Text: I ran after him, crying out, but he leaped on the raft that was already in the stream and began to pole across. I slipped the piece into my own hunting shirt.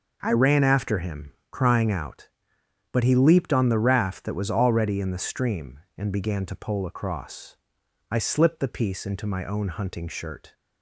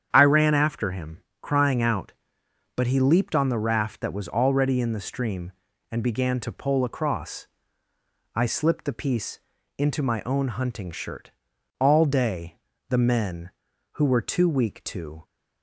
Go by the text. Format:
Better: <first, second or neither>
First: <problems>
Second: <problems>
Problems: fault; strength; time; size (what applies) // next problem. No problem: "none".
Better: first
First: none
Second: starts louder than the rest; strong; until 1.1 s; 8.5 dB // pauses between "piece" and "into"; at 9.3 s; 0.40 s long // goes on to say "All day the men who were too weak to"; strong; from 11.7 s on; 3.4 s long